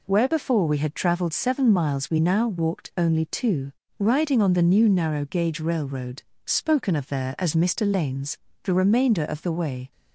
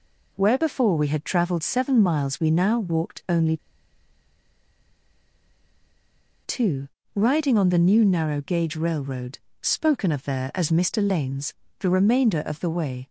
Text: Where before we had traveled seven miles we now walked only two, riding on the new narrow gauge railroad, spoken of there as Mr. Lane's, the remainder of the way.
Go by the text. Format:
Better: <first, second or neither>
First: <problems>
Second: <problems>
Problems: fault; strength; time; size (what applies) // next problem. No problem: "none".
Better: first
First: none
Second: pauses between "only" and "two"; strong; at 3.5 s; 2.8 s long